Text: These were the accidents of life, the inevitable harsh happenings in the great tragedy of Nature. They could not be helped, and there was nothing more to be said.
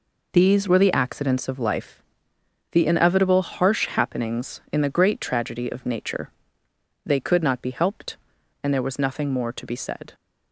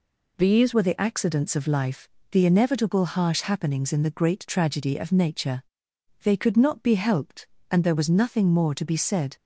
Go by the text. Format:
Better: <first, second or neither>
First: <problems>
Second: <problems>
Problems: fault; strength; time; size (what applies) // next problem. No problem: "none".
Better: first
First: none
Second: changes voice at "were"; from 0.7 s on; 8.6 s long